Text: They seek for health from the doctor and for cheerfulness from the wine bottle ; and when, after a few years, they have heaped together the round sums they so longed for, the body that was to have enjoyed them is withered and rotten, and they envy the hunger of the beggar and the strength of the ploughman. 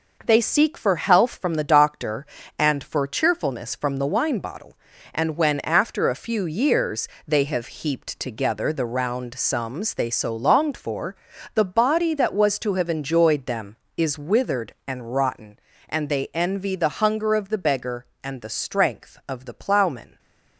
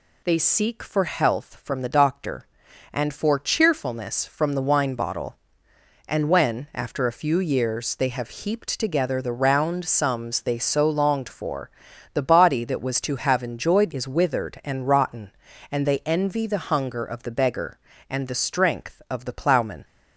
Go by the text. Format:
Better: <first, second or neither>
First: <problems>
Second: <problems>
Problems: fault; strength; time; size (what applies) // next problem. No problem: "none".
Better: first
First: none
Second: skips "them"; at 13.9 s